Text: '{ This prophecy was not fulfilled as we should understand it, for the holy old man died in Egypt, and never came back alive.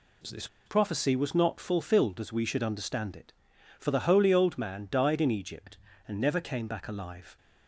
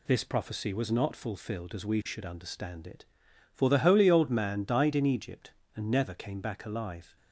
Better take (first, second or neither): second